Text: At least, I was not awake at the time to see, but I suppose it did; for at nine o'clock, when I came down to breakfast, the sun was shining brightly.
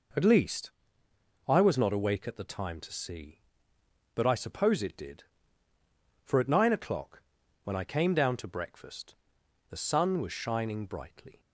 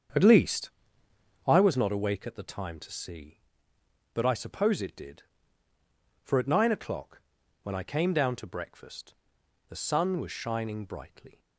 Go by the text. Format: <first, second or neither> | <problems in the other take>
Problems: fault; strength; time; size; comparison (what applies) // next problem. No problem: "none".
first | starts louder than the rest; strong; until 1.7 s; 7.5 dB